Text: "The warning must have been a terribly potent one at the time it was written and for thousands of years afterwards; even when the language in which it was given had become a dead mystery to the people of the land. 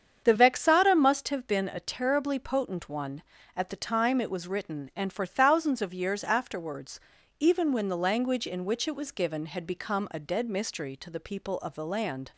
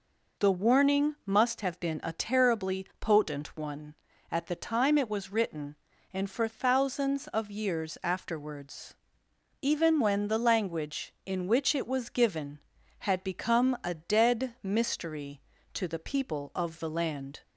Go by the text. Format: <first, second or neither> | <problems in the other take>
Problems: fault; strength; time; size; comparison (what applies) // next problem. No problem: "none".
second | starts louder than the rest; strong; until 1.2 s; 7.5 dB // says "vexata" for "warning"; at 0.3 s